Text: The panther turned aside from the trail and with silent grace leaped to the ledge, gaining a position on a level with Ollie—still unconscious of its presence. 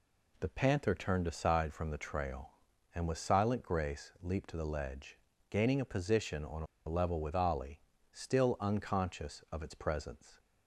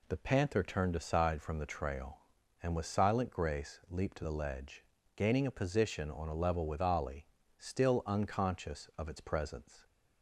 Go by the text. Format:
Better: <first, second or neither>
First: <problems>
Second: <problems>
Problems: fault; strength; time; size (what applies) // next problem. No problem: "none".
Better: second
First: pauses between "a" and "level"; slight; at 6.6 s; 0.22 s long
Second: none